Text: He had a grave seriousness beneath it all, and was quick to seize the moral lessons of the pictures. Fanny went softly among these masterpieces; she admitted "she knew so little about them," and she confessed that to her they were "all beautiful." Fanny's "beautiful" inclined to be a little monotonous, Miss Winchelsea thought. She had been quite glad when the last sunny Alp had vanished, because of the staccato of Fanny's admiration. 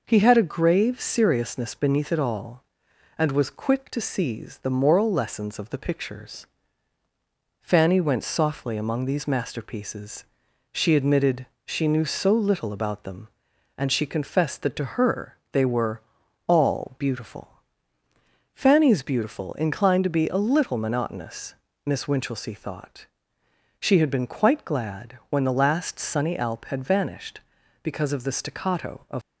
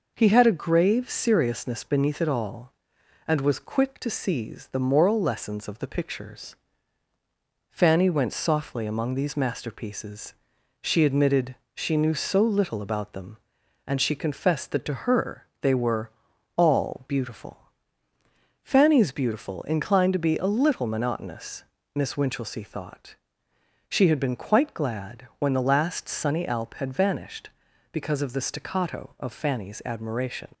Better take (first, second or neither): second